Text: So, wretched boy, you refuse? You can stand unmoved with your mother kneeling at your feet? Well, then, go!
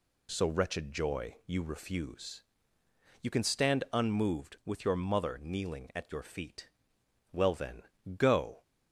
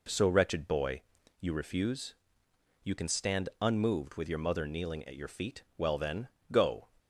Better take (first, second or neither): second